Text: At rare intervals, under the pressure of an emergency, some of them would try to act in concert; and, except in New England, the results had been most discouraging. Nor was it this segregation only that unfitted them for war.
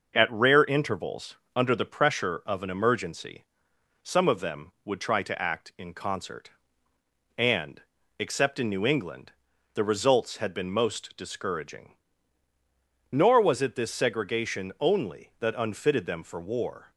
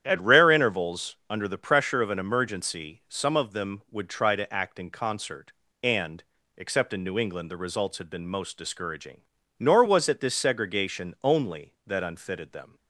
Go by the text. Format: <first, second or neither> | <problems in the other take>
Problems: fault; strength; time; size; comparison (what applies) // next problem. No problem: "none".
first | starts louder than the rest; strong; until 1.0 s; 10 dB // stops before "for war"; at 12.7 s